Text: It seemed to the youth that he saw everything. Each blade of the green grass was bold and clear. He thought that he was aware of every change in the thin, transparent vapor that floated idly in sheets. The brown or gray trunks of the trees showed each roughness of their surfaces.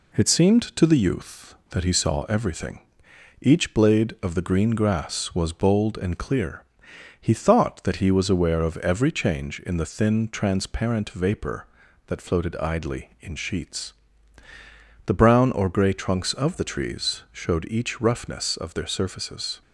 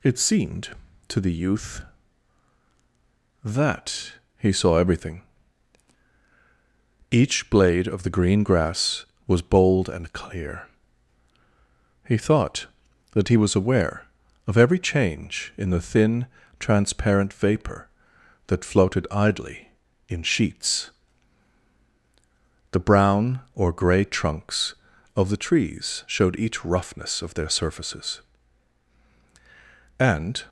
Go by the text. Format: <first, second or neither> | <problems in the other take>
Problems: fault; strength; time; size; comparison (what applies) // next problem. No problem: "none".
first | pauses between "that" and "he"; slight; at 4.1 s; 0.26 s long // goes on to say "And"; slight; from 29.9 s on; 0.46 s long